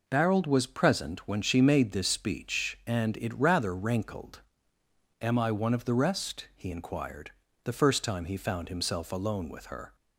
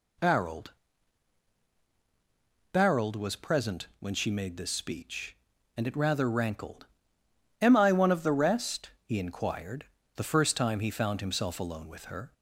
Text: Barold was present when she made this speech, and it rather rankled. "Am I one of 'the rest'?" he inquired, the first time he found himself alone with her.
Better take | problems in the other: first | says "Barold" twice; at 2.7 s

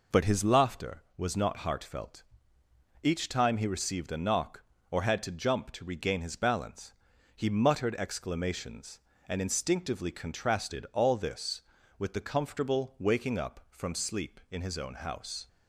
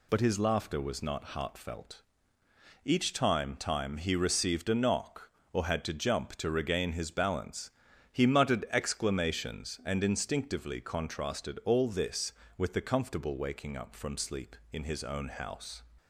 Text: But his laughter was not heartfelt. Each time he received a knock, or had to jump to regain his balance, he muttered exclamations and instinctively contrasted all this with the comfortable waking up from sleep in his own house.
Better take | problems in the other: first | says "time" twice; at 3.5 s

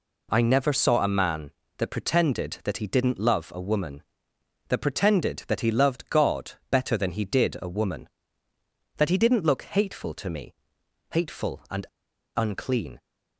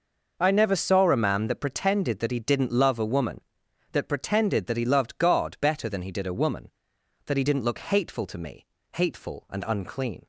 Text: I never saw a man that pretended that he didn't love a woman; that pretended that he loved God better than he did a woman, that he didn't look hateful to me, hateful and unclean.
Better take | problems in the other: second | pauses between "God" and "better"; slight; at 6.5 s; 0.18 s long // pauses between "and" and "unclean"; noticeable; at 11.8 s; 0.52 s long

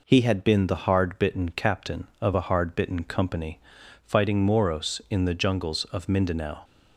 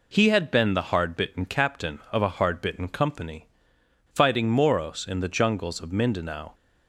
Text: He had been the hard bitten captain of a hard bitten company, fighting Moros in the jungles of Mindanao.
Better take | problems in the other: neither | none

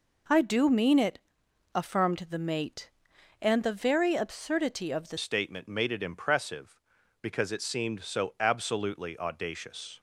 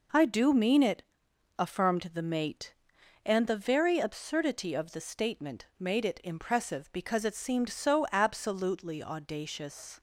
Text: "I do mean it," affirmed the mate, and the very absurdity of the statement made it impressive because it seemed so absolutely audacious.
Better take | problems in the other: second | changes voice at "statement"; from 5.1 s on; 4.8 s long

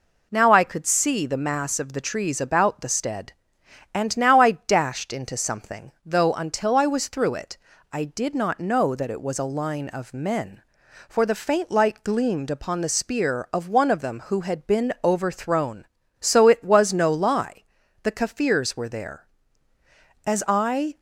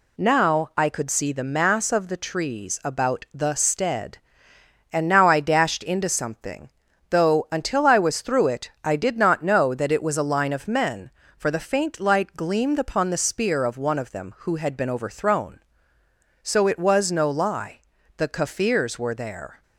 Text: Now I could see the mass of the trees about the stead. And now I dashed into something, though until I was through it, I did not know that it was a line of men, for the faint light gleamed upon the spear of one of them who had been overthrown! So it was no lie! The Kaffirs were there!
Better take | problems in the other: second | goes on to say "As I"; noticeable; from 20.2 s on; 0.72 s long

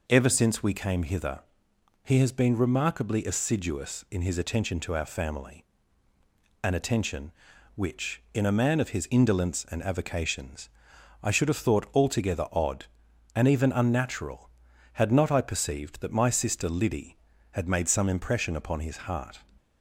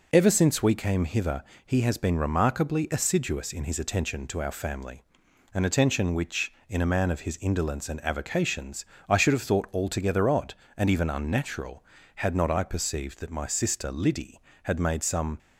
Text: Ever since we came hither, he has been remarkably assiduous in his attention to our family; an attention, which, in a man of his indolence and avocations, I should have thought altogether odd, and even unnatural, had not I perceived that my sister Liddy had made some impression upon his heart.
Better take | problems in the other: first | stops before "impression upon his heart"; at 15.3 s

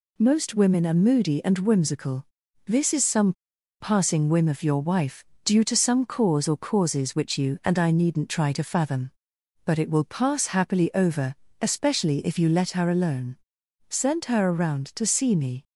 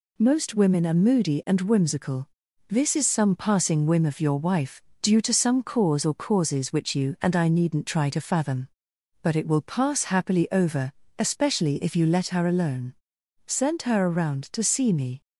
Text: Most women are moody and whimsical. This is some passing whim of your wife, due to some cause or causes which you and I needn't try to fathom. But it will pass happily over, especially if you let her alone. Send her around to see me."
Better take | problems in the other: second | pauses between "some" and "passing"; noticeable; at 3.3 s; 0.48 s long

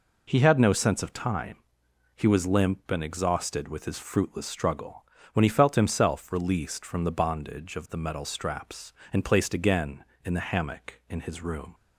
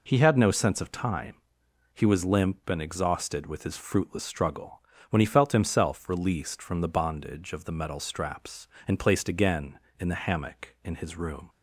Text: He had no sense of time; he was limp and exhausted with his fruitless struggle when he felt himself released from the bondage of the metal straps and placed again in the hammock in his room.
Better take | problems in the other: neither | pauses between "struggle" and "when"; slight; the same in both

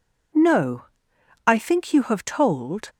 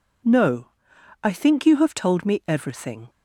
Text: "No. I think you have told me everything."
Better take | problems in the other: second | stops before "me everything"; at 2.8 s

